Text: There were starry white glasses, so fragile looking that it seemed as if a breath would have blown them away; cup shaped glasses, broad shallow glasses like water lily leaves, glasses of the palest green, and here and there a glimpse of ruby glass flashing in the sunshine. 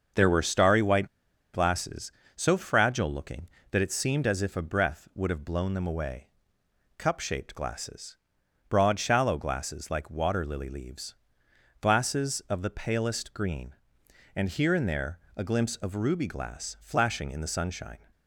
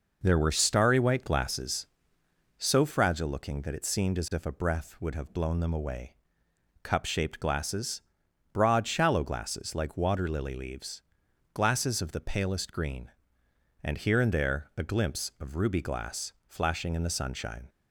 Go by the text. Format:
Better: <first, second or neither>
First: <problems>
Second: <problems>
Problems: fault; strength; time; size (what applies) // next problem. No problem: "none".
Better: second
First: starts louder than the rest; until 1.6 s; 6 dB // pauses between "white" and "glasses"; noticeable; at 1.0 s; 0.46 s long // pauses between "there" and "a"; slight; at 15.1 s; 0.20 s long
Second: none